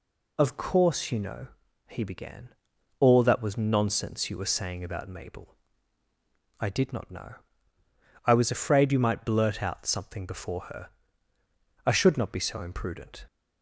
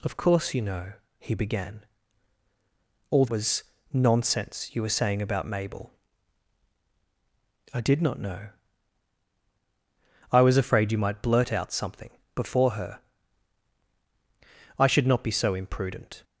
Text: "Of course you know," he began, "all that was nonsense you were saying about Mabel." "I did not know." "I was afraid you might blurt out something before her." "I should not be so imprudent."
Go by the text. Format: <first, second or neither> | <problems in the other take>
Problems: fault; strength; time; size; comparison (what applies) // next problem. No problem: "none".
first | skips "that"; at 3.2 s // pauses between "was" and "nonsense"; slight; at 3.6 s; 0.30 s long // pauses between "something" and "before"; slight; at 12.0 s; 0.26 s long